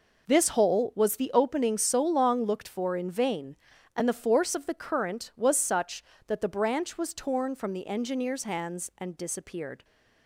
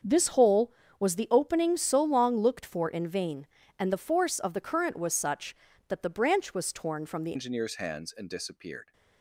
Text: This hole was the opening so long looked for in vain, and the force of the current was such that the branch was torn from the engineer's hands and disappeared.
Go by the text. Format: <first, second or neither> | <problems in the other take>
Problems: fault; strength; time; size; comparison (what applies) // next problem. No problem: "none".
first | starts louder than the rest; until 1.3 s; 6.5 dB // changes voice at "engineer's"; from 7.3 s on; 1.6 s long